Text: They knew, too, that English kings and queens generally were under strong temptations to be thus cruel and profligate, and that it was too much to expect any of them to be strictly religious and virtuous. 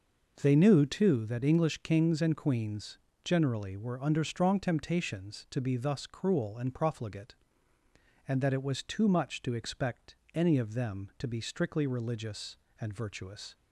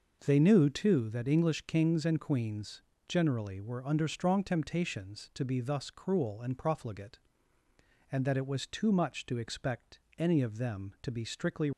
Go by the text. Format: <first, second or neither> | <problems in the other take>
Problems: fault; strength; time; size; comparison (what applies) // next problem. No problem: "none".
first | pauses between "queens" and "generally"; slight; at 2.8 s; 0.26 s long; slight in the first // pauses between "expect" and "any"; slight; at 10.0 s; 0.18 s long; slight in the first // stops before "religious and virtuous"; at 11.7 s